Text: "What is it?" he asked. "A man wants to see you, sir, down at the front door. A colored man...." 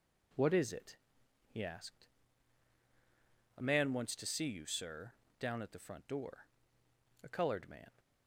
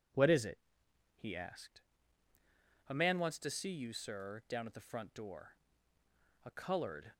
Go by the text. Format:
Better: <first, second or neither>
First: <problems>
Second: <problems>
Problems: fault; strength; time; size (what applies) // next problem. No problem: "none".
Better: first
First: none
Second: stops before "man"; at 7.1 s